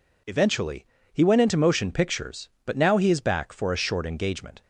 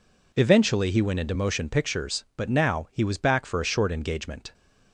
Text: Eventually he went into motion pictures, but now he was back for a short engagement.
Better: second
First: pauses between "Eventually" and "he"; slight; at 0.8 s; 0.26 s long // says "is" for "was"; at 3.1 s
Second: none

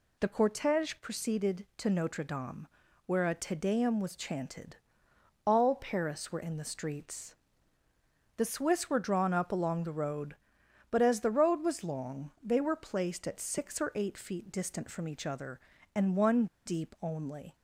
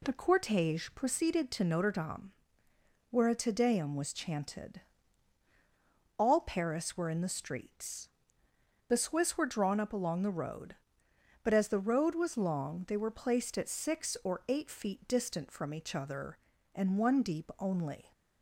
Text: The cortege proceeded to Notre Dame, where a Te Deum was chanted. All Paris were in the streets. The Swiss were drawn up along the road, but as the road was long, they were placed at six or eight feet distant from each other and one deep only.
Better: second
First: pauses between "one" and "deep"; slight; at 16.4 s; 0.19 s long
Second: none

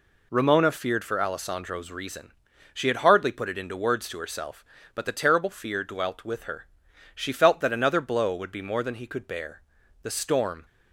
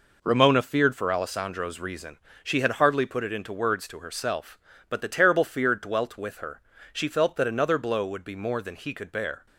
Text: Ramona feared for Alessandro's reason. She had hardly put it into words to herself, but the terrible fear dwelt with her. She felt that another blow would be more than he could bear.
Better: second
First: goes on to say "The storm"; noticeable; from 10.0 s on; 0.62 s long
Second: none

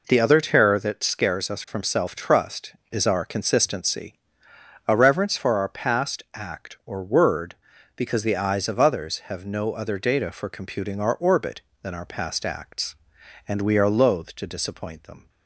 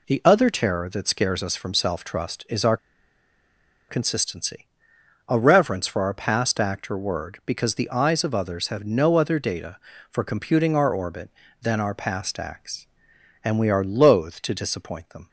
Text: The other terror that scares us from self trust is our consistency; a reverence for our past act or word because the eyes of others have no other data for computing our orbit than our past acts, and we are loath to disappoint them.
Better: first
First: none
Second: pauses between "our" and "consistency"; at 2.7 s; 1.1 s long

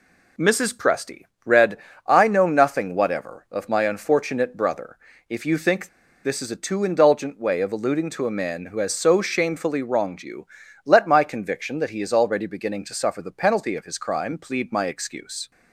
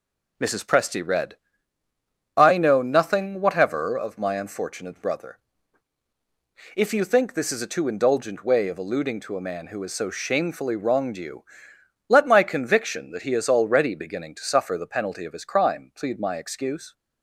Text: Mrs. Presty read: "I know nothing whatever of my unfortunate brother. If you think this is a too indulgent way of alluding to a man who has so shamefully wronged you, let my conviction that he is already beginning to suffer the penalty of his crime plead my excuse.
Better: second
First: pauses between "Presty" and "read"; slight; at 1.2 s; 0.24 s long // pauses between "think" and "this"; at 5.8 s; 0.37 s long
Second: none

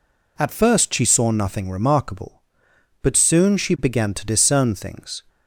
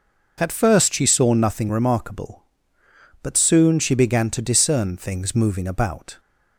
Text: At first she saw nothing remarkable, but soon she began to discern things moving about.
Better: second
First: stops before "moving about"; at 5.2 s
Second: none

